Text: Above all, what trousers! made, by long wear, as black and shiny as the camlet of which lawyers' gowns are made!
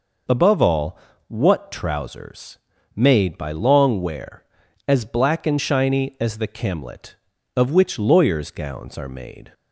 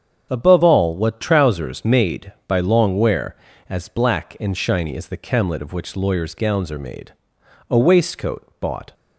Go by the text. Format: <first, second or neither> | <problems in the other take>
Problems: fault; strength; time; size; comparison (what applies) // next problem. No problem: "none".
first | starts louder than the rest; strong; until 1.3 s; 7.5 dB // goes on to say "A waistcoat bought"; noticeable; from 7.6 s on; 1.2 s long